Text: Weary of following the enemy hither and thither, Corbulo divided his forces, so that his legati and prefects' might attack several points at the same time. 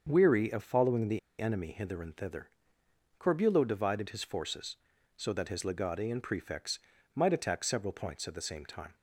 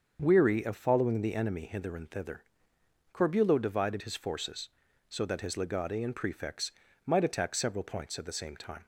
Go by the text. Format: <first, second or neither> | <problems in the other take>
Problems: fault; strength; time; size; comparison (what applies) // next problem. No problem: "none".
second | starts louder than the rest; until 1.1 s; 6.5 dB; also in the second // pauses between "the" and "enemy"; slight; at 1.1 s; 0.19 s long // pauses between "prefects" and "might"; slight; at 6.8 s; 0.34 s long; slight in the second